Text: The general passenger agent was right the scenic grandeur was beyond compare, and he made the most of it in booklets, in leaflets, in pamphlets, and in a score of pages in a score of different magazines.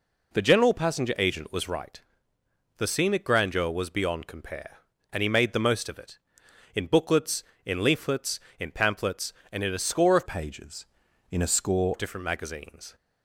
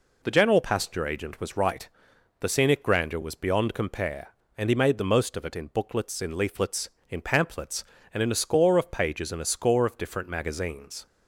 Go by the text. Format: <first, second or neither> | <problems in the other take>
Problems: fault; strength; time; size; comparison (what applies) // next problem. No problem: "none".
second | pauses between "right" and "the"; noticeable; at 1.9 s; 0.78 s long; noticeable in the second // changes voice from "pages" to "score"; from 10.2 to 11.9 s; 1.7 s long